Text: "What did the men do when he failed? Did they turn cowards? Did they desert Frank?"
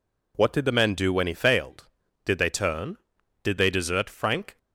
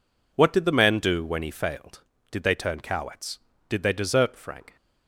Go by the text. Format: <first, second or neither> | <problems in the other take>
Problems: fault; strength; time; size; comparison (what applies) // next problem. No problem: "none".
second | skips "cowards"; at 3.1 s